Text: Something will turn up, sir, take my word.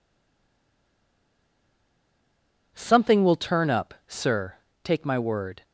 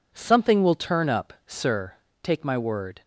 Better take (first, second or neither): second